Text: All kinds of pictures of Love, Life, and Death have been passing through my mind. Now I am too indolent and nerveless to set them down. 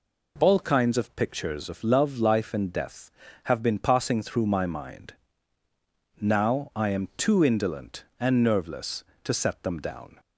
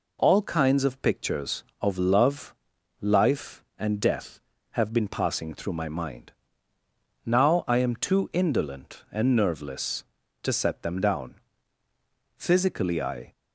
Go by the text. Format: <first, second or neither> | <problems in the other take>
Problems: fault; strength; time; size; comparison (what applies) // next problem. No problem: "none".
first | goes on to say "Physically I"; noticeable; from 12.3 s on; 0.94 s long